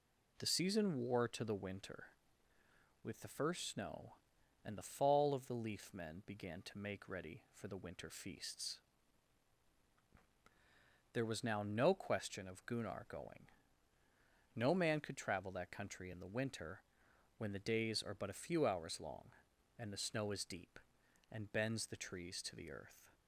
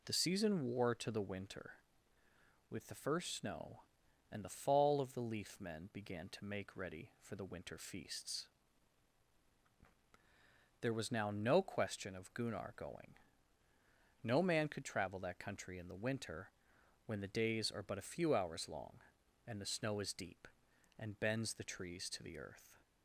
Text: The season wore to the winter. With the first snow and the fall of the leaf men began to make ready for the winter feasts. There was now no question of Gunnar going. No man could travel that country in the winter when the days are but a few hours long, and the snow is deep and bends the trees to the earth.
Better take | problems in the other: neither | pauses between "winter" and "when"; noticeable; the same in both

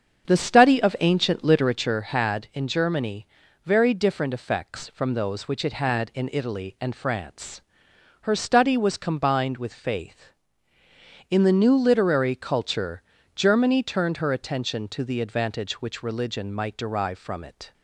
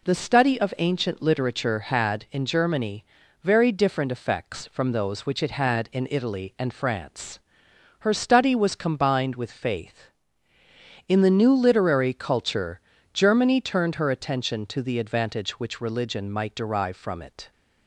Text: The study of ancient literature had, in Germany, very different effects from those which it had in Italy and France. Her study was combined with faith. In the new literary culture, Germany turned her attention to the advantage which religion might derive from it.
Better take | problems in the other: second | starts louder than the rest; strong; until 2.0 s; 7 dB

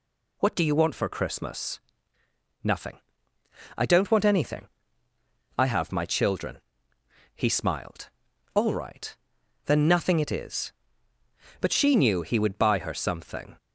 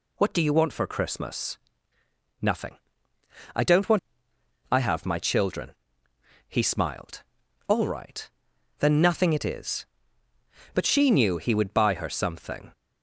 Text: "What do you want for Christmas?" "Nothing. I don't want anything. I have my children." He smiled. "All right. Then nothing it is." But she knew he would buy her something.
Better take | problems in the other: first | skips "anything"; at 4.3 s

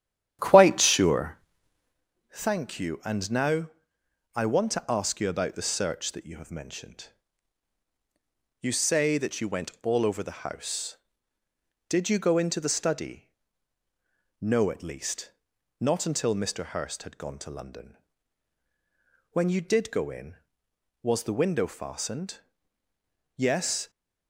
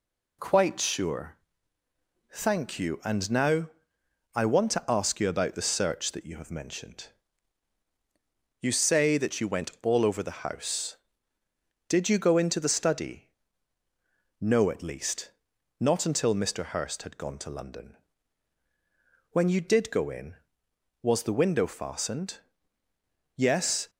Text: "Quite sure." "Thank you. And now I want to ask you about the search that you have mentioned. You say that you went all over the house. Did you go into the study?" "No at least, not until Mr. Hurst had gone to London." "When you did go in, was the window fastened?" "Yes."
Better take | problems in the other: second | starts louder than the rest; strong; until 2.0 s; 10.5 dB // pauses between "now" and "I"; noticeable; at 3.6 s; 0.64 s long; noticeable in the second

